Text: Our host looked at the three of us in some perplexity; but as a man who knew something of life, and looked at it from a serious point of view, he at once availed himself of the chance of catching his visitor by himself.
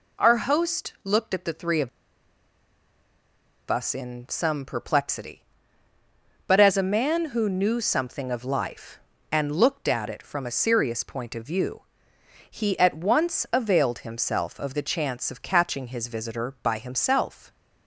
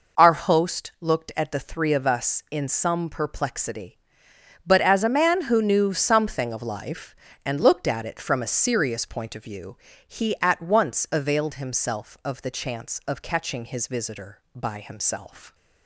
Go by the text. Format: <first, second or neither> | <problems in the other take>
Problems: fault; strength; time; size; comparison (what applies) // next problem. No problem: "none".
second | pauses between "of" and "us"; strong; at 1.8 s; 1.8 s long